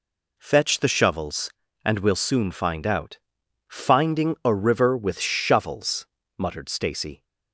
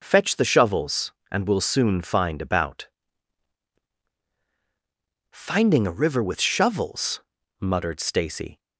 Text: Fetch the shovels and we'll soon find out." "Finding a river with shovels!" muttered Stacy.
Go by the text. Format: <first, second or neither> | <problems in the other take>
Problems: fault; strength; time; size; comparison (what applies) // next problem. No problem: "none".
first | says "about" for "out"; at 2.4 s